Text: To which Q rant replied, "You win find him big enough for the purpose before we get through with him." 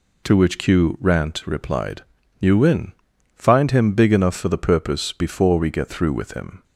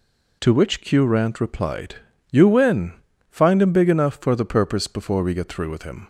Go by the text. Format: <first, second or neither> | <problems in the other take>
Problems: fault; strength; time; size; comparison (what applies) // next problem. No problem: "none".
neither | pauses between "win" and "find"; the same in both